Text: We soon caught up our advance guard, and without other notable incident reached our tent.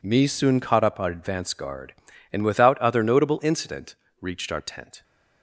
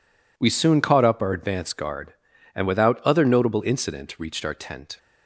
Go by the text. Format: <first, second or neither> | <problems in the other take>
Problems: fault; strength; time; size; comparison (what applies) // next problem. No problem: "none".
second | says "Me" for "We"; at 0.0 s // pauses between "incident" and "reached"; slight; at 3.9 s; 0.24 s long